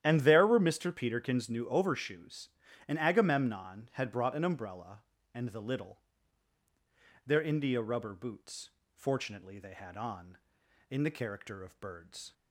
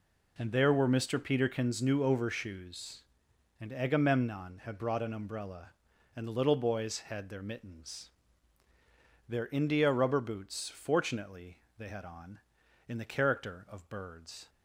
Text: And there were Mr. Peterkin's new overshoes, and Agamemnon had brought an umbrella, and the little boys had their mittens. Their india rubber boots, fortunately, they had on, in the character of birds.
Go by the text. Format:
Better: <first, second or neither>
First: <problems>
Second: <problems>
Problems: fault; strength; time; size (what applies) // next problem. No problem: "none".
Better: second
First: starts louder than the rest; strong; until 1.0 s; 11 dB // skips "boys had their mittens"; at 6.6 s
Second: none